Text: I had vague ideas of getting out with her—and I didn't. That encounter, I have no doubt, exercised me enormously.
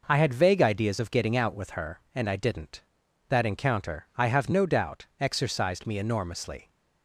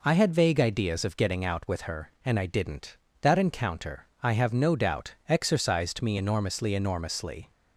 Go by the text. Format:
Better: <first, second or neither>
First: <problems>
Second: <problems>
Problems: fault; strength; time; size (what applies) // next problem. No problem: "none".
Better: first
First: none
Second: says "enormously" twice; at 6.7 s